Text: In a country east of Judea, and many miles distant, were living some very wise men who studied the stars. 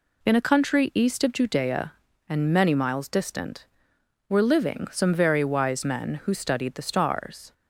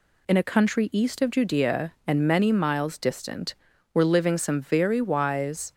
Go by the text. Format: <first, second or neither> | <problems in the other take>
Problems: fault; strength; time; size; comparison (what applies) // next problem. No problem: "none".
first | stops before "men who studied the stars"; at 5.7 s